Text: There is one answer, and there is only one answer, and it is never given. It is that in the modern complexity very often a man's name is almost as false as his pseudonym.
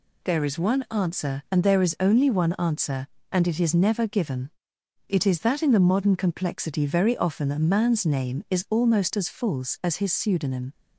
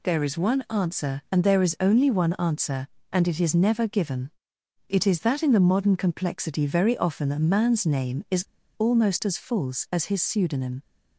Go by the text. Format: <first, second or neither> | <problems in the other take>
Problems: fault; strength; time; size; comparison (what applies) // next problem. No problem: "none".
first | pauses between "is" and "almost"; slight; at 8.4 s; 0.32 s long